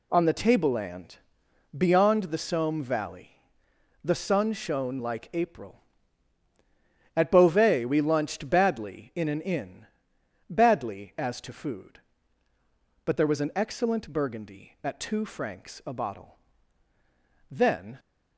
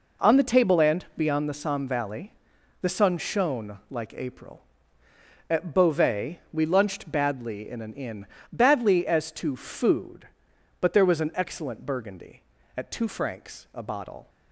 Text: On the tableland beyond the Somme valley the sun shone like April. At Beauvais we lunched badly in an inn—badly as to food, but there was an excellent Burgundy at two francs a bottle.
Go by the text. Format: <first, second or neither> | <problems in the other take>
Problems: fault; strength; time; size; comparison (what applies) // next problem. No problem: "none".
second | pauses between "tableland" and "beyond"; noticeable; at 1.1 s; 0.58 s long // pauses between "valley" and "the"; noticeable; at 3.4 s; 0.62 s long; noticeable in the second // goes on to say "Then"; slight; from 17.5 s on; 0.48 s long